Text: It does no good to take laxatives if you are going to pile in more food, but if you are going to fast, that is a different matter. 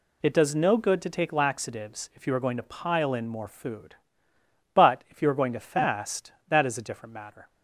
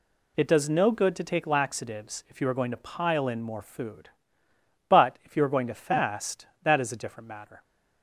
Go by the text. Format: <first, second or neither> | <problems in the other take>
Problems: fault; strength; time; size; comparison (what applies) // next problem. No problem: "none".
neither | none